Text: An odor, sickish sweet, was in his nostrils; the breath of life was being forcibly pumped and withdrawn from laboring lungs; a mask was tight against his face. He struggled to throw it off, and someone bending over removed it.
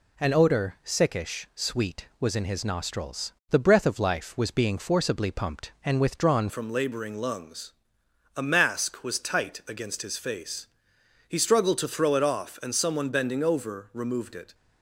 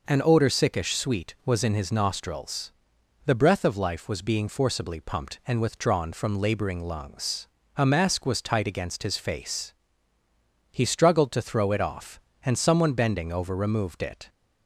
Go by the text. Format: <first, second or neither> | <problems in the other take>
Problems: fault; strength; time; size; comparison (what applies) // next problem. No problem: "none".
second | changes voice at "from"; from 6.4 s on; 8.1 s long